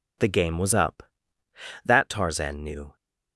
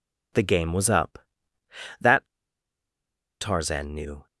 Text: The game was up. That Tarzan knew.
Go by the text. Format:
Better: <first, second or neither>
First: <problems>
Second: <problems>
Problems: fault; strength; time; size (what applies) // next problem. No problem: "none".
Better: first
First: none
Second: pauses between "That" and "Tarzan"; at 2.2 s; 1.1 s long